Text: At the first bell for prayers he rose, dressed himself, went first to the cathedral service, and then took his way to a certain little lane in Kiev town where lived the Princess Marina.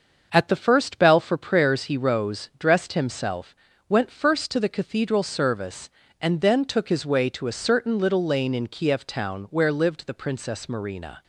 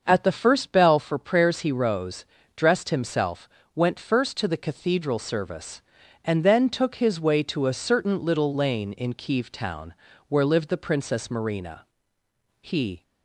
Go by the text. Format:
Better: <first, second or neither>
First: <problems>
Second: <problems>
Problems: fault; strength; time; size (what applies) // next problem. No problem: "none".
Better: first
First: starts louder than the rest; until 1.3 s; 6.5 dB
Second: starts louder than the rest; until 1.0 s; 6.5 dB // pauses between "town" and "where"; slight; at 9.9 s; 0.34 s long // goes on to say "He"; slight; from 12.6 s on; 0.42 s long